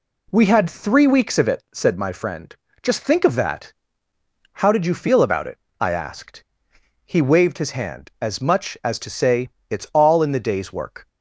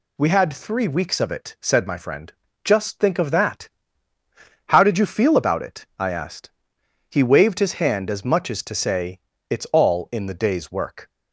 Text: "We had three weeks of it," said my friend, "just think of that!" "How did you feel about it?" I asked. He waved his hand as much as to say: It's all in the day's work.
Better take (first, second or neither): neither